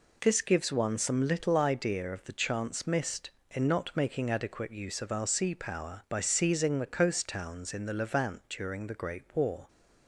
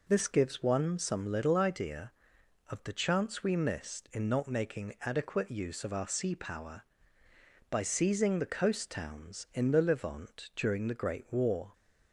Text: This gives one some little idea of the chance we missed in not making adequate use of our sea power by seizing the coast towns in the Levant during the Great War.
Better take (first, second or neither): second